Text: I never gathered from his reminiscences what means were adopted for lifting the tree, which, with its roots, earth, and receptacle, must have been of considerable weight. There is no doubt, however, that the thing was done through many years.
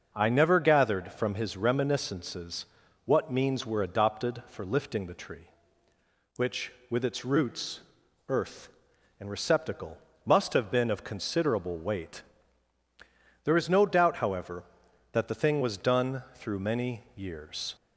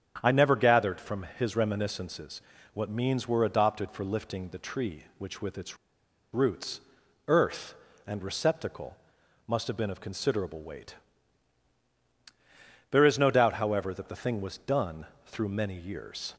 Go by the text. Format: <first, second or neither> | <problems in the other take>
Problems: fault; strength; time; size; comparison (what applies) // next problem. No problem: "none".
first | starts louder than the rest; strong; until 1.2 s; 8.5 dB // pauses between "reminiscences" and "what"; slight; at 2.4 s; 0.32 s long; also in the first // pauses between "its" and "roots"; noticeable; at 5.7 s; 0.57 s long // pauses between "done" and "through"; slight; at 15.0 s; 0.18 s long